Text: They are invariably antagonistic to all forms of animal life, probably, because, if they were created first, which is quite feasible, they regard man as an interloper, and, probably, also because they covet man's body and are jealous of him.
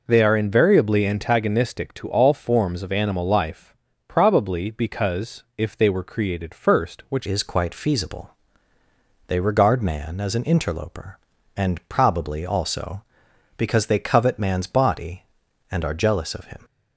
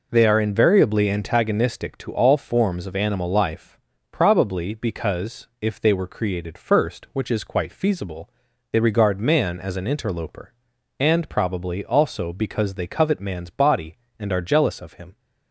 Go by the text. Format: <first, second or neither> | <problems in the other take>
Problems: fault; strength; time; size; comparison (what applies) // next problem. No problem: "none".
second | changes voice at "is"; from 7.2 s on; 9.4 s long